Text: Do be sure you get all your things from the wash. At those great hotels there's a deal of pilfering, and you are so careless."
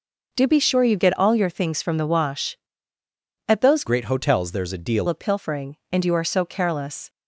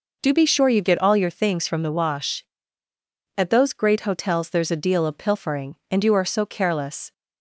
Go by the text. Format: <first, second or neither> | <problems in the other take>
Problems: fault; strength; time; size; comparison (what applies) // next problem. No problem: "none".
second | changes voice from "great" to "deal"; from 3.8 to 5.0 s; 1.2 s long